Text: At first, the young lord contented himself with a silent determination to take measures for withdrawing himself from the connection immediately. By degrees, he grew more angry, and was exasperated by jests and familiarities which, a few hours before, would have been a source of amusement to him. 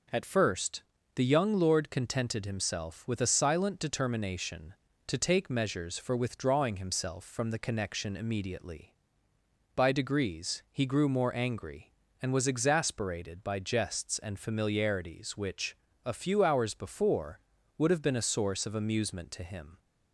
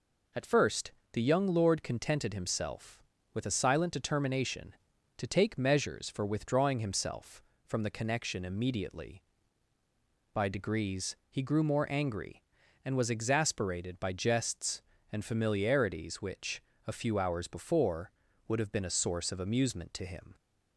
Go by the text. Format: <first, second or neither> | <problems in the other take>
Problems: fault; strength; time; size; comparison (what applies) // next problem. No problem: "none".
neither | none